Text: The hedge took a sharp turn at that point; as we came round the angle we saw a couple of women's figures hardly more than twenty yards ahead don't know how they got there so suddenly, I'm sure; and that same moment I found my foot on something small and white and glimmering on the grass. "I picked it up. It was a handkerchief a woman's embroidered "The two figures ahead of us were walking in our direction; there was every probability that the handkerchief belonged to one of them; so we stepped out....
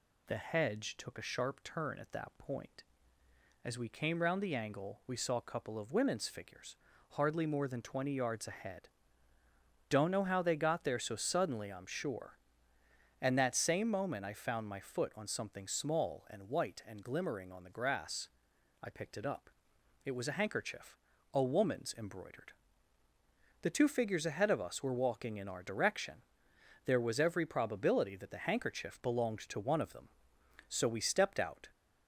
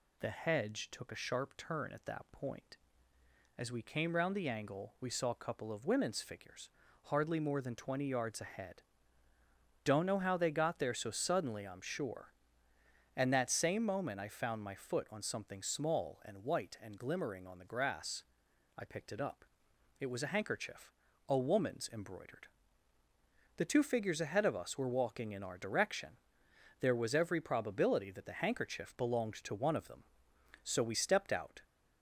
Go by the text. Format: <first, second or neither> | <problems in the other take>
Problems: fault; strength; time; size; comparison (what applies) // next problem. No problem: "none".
neither | pauses between "figures" and "hardly"; slight; the same in both // pauses between "ahead" and "don't"; the same in both // pauses between "handkerchief" and "a"; slight; the same in both // pauses between "embroidered" and "The"; the same in both